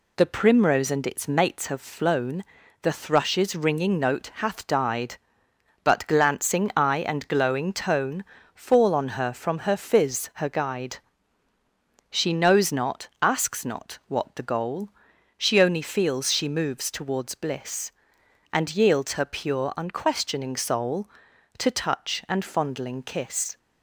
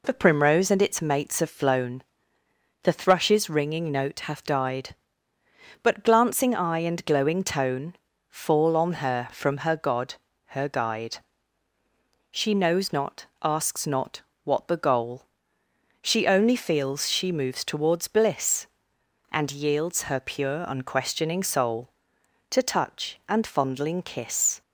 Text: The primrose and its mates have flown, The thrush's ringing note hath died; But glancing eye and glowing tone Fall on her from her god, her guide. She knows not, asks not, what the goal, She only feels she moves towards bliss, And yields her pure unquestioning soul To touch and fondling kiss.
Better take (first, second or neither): second